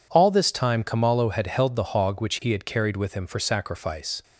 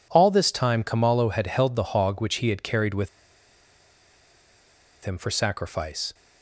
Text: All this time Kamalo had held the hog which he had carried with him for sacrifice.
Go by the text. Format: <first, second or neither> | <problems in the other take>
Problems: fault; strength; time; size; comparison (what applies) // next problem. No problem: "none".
first | pauses between "with" and "him"; strong; at 3.0 s; 1.9 s long